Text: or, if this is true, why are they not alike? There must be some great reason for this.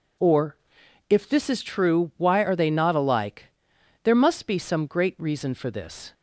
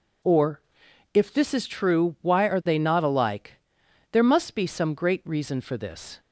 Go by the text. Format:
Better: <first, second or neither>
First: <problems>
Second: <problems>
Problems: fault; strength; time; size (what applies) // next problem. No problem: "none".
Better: neither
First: none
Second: none